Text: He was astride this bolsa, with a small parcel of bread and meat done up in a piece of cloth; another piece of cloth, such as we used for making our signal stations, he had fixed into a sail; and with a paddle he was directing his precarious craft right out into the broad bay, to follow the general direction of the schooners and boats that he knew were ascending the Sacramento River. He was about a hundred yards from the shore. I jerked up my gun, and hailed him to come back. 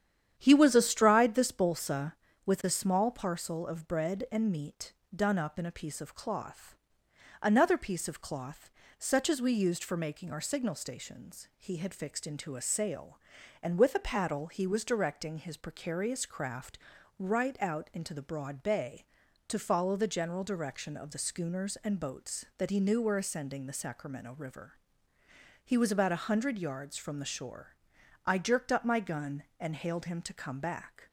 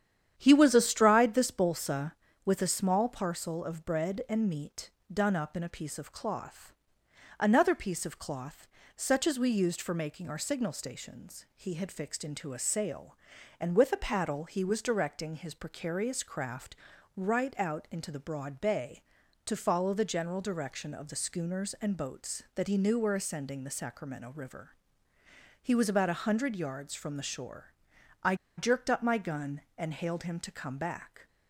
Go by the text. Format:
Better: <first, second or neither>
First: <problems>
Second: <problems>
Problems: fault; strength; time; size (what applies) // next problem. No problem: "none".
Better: first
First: starts louder than the rest; strong; until 1.3 s; 9.5 dB // pauses between "meat" and "done"; slight; at 4.9 s; 0.22 s long // pauses between "craft" and "right"; at 16.7 s; 0.40 s long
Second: starts louder than the rest; strong; until 1.3 s; 9.5 dB // pauses between "meat" and "done"; slight; at 4.9 s; 0.22 s long // pauses between "craft" and "right"; at 16.7 s; 0.40 s long // pauses between "I" and "jerked"; slight; at 28.3 s; 0.23 s long